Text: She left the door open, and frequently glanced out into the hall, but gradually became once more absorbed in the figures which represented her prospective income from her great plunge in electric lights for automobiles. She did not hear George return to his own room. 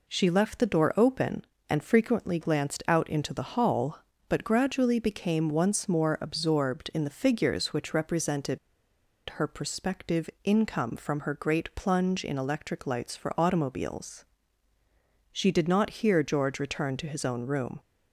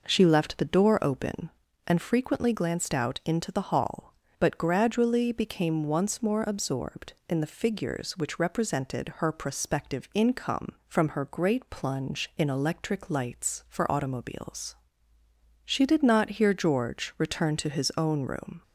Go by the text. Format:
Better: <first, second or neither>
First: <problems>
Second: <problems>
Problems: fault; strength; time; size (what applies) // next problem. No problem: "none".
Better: second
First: pauses between "represented" and "her"; noticeable; at 8.5 s; 0.71 s long // pauses between "prospective" and "income"; slight; at 10.2 s; 0.16 s long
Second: none